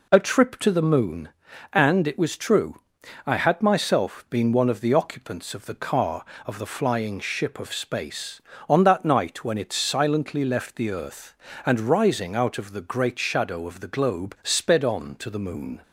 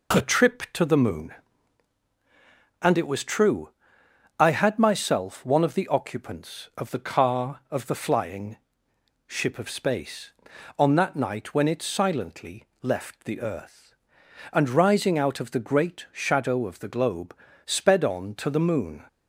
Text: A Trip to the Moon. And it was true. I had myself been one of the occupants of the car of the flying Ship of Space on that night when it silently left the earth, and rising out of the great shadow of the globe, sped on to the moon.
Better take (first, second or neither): first